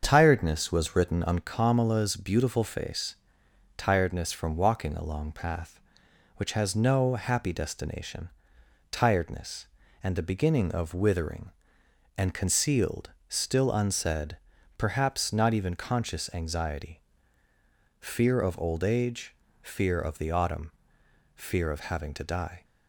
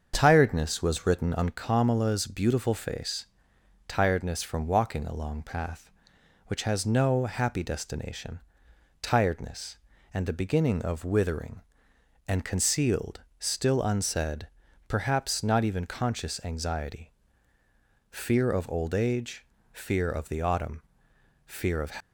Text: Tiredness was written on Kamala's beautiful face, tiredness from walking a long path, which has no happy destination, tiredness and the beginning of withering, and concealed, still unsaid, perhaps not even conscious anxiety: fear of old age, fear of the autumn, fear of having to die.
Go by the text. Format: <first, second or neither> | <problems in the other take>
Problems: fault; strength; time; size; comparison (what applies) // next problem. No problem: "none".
first | starts louder than the rest; until 1.1 s; 7 dB; also in the first // stops before "having to die"; at 21.9 s